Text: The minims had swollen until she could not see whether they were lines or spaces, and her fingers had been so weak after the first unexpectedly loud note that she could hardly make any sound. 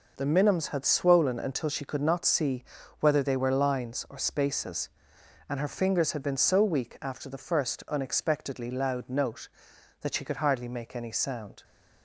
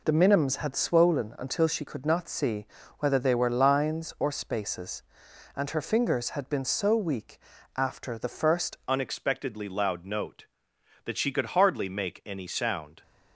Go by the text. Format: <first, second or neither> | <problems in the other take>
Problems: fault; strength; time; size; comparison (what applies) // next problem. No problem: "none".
first | pauses between "see" and "whether"; slight; at 2.6 s; 0.34 s long; slight in the first // pauses between "weak" and "after"; at 7.3 s; 0.38 s long // changes voice at "unexpectedly"; from 8.8 s on; 4.2 s long